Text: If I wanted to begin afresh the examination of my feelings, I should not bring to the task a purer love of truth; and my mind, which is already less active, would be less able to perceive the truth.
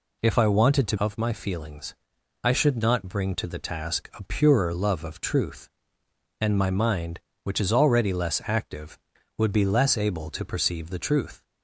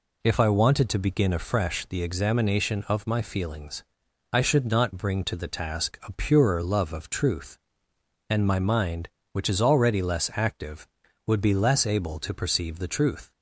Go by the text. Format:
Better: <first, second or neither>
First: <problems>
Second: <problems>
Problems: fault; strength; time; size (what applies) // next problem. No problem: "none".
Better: second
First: skips "begin afresh the examination"; at 0.9 s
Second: none